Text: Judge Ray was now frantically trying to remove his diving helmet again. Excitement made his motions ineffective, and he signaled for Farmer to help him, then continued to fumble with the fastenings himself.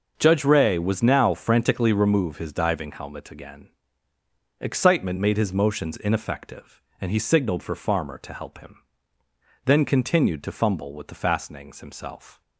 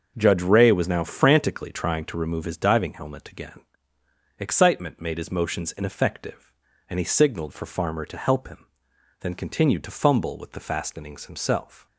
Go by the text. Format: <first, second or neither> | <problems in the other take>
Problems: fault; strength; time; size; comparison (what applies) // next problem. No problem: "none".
second | starts louder than the rest; noticeable; until 1.1 s; 6 dB; also in the second // skips "trying to"; at 1.9 s